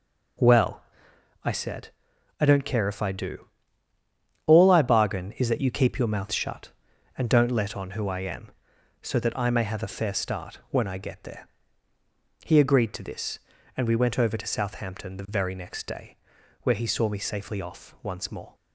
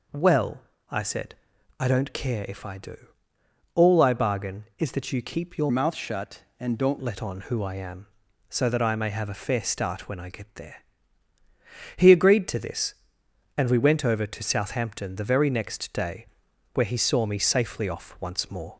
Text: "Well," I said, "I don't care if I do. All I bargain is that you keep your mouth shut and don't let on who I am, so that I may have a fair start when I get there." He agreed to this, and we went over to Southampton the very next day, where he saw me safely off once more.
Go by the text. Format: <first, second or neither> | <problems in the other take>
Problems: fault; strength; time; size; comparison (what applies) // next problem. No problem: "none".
first | changes voice from "mouth" to "don't"; from 5.7 to 6.9 s; 1.2 s long